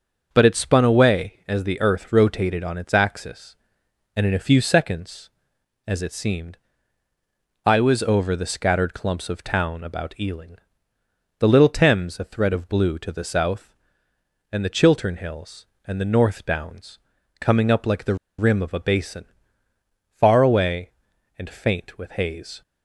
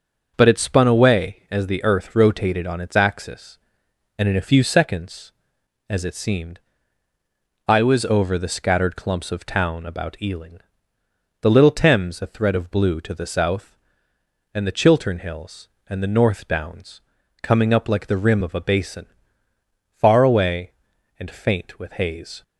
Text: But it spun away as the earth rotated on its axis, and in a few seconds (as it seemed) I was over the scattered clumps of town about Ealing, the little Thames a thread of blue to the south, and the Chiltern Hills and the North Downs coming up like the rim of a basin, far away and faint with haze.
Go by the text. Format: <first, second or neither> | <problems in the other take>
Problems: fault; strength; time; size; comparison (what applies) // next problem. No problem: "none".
second | starts louder than the rest; until 1.3 s; 6.5 dB; also in the second // pauses between "Downs" and "coming"; at 16.9 s; 0.42 s long; also in the second // pauses between "the" and "rim"; slight; at 18.1 s; 0.23 s long